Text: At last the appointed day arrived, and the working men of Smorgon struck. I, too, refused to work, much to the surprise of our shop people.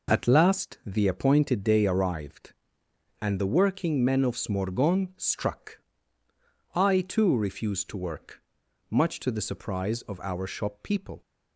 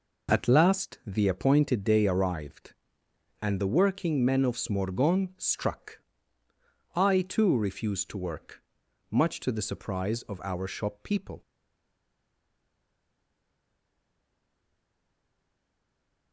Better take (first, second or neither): first